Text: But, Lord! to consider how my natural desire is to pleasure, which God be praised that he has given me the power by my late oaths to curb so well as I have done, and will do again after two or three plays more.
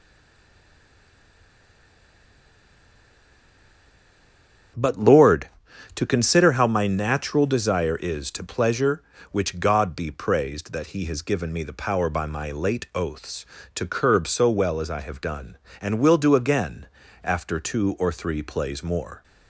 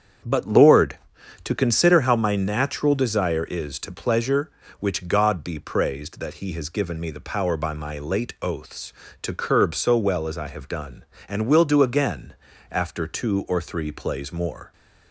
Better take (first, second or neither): second